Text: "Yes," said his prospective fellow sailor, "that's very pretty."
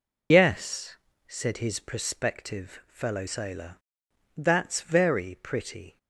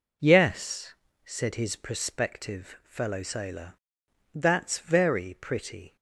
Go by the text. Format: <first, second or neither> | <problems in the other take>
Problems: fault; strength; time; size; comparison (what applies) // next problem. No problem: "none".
second | loses the start of "Yes"; at 0.3 s; 60 ms